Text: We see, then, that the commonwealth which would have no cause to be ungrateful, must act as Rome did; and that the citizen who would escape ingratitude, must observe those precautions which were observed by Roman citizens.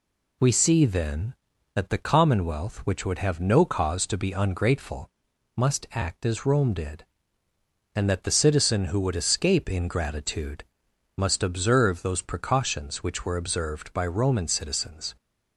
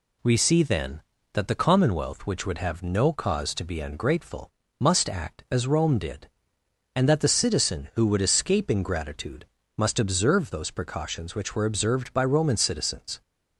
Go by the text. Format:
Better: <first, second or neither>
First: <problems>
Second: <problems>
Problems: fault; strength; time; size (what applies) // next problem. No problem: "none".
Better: neither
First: none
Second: none